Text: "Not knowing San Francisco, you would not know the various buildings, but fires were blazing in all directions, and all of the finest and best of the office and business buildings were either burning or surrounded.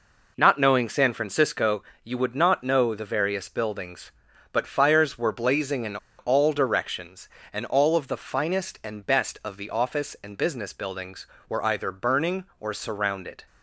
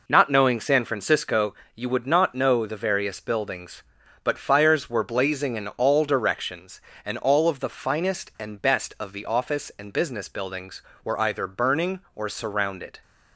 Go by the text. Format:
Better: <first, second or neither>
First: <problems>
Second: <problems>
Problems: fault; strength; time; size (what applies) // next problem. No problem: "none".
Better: second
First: pauses between "in" and "all"; slight; at 5.9 s; 0.24 s long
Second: none